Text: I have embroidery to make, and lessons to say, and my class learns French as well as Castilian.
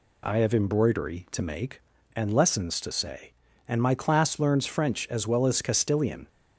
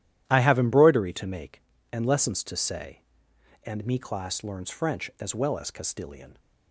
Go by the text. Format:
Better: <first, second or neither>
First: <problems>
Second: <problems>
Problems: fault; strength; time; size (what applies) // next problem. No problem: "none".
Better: first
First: none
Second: starts louder than the rest; strong; until 1.2 s; 12 dB // says "me" for "my"; at 3.8 s